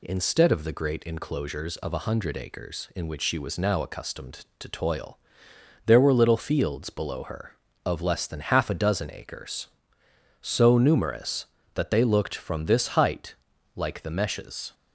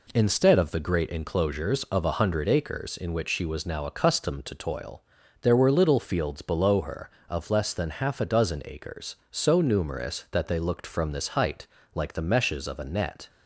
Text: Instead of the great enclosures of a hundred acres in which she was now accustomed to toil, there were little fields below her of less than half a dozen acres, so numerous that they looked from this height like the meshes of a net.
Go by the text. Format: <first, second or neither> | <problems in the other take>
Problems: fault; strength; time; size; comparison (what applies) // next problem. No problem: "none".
second | pauses between "height" and "like"; at 13.3 s; 0.42 s long; slight in the second // stops before "of a net"; at 14.7 s